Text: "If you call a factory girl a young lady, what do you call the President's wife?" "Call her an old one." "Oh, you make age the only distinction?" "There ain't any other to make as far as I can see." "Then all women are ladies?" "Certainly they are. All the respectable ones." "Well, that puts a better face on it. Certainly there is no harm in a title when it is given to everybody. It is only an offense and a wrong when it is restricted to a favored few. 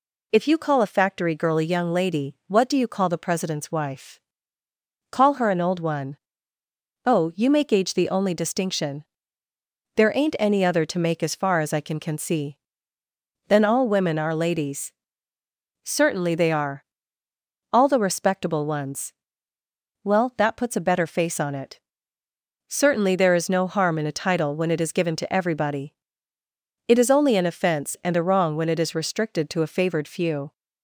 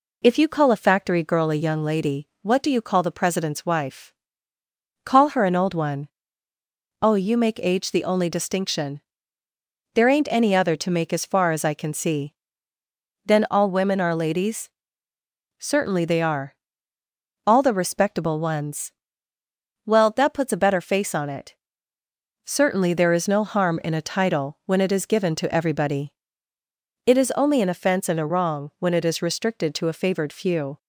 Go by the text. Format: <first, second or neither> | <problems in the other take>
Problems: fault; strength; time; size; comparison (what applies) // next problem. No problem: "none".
second | says "can" twice; at 12.0 s